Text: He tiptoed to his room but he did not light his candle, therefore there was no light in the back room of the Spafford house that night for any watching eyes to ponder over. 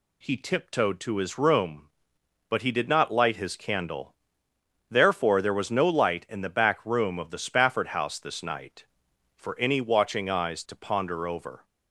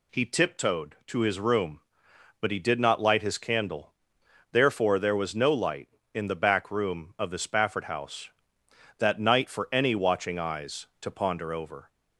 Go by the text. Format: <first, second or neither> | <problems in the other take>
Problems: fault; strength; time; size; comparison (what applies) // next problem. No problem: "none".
second | says "this" for "that"; at 8.1 s